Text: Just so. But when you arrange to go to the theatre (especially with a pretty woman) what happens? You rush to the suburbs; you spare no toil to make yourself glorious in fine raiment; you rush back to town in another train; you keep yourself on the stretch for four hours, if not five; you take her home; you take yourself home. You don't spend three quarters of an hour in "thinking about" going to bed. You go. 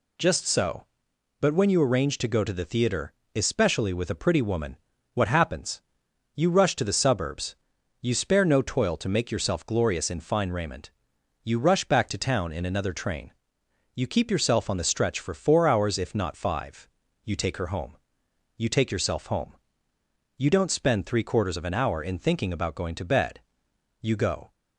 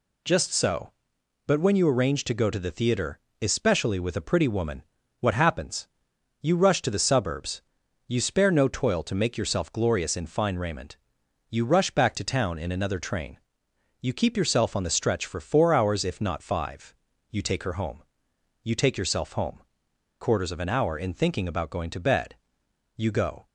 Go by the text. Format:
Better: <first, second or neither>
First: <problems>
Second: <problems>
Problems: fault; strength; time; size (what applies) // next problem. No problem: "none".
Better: first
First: none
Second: skips "You don't spend three"; at 19.9 s